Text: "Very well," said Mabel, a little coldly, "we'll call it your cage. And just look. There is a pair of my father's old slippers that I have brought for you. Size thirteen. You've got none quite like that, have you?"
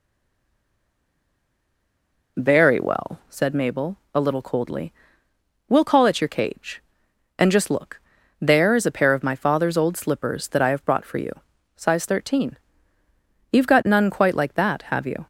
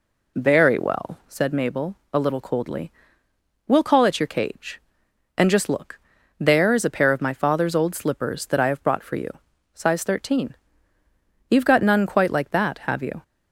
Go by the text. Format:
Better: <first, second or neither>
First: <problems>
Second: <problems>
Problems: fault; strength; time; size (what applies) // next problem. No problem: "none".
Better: second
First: stays silent before the first word; until 2.3 s; 2.3 s long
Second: none